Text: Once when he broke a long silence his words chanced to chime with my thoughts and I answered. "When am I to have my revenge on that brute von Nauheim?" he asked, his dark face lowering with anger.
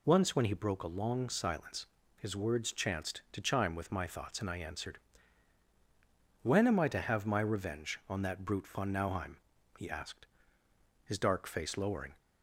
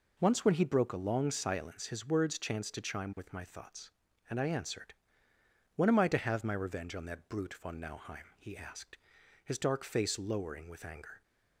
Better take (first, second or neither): second